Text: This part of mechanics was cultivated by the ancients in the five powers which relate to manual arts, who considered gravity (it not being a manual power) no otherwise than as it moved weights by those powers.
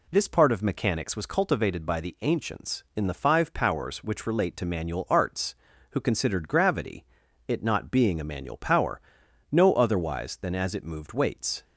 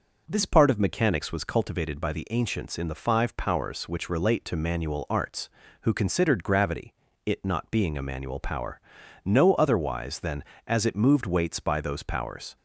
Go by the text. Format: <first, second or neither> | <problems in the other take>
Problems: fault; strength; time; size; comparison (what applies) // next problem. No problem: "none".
second | stops before "by those powers"; at 11.6 s